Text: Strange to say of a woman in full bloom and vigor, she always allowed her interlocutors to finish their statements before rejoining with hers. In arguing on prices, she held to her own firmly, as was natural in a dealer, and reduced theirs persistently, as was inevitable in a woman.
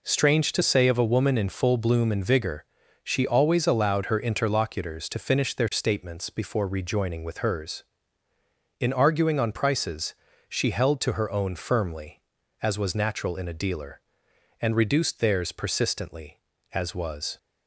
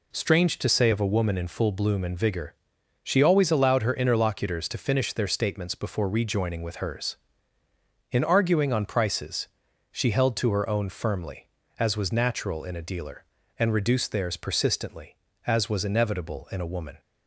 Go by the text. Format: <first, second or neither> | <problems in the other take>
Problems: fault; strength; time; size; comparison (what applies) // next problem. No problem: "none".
second | stops before "inevitable in a woman"; at 17.3 s